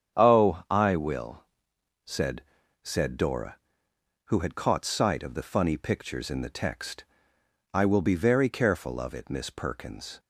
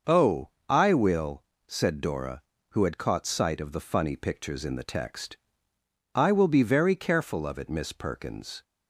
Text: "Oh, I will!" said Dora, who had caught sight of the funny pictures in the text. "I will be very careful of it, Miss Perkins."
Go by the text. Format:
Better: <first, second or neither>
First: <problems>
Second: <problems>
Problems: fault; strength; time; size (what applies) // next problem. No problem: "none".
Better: second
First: starts louder than the rest; strong; until 1.2 s; 8 dB // says "said" twice; at 2.8 s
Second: starts louder than the rest; noticeable; until 1.2 s; 6 dB